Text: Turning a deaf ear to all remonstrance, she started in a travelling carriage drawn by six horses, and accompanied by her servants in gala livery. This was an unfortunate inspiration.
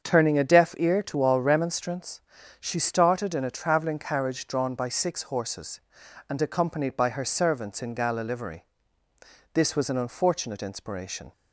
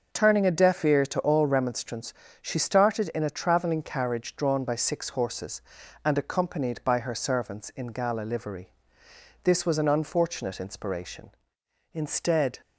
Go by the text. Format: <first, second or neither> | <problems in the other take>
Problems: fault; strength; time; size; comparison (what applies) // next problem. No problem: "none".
first | starts louder than the rest; noticeable; until 1.1 s; 6 dB; also in the first // goes on to say "Instead"; noticeable; from 11.9 s on; 0.66 s long